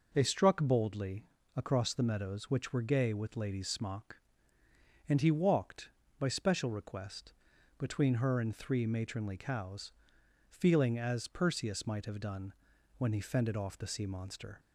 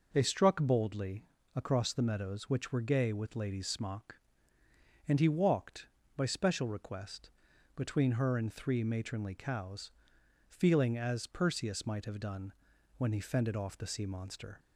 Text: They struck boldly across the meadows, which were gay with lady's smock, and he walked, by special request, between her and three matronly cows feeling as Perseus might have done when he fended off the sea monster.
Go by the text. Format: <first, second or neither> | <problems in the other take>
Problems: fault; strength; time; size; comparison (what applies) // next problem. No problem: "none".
neither | pauses between "boldly" and "across"; slight; the same in both // pauses between "cows" and "feeling"; noticeable; the same in both // pauses between "done" and "when"; noticeable; the same in both